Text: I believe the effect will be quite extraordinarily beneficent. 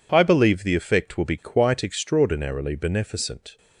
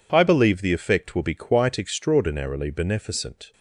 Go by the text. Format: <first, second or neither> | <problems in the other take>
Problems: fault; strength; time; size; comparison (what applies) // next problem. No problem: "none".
neither | none